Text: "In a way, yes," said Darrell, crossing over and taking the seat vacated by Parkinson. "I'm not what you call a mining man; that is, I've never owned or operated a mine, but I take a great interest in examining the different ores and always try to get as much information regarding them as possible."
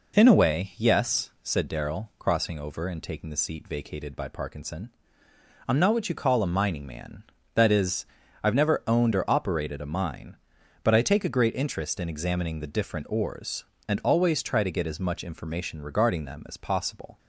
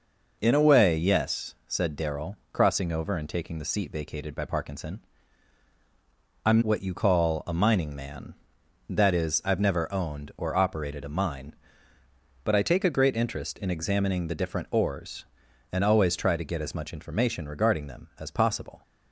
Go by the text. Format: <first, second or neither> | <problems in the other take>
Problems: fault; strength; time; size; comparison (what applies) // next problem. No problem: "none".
first | skips "not"; at 6.6 s